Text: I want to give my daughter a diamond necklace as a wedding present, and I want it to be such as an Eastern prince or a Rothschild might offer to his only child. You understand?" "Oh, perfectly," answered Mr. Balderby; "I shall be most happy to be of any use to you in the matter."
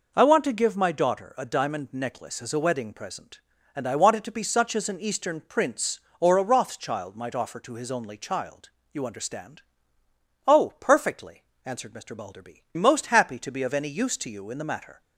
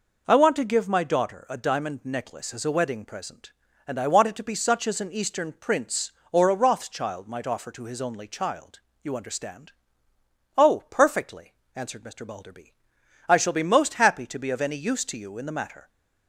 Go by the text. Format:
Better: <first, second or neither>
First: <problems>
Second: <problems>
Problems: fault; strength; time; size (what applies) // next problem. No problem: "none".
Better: second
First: skips "I shall be"; at 12.6 s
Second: none